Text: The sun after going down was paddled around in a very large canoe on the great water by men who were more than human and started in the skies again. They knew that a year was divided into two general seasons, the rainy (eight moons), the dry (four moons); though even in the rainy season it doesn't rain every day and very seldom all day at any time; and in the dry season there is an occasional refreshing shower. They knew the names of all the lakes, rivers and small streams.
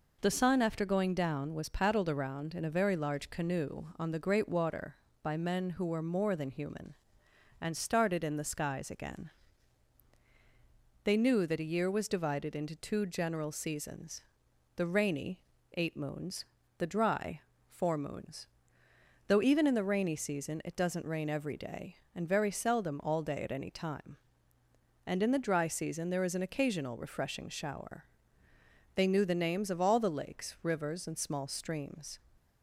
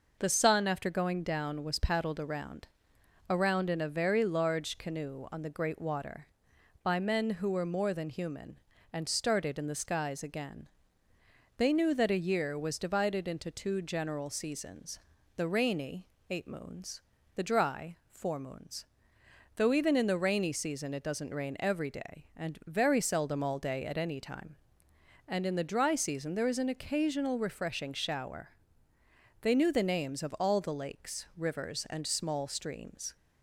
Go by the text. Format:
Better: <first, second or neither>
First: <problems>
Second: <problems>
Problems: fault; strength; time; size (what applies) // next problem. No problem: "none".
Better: first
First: none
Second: says "around" twice; at 3.2 s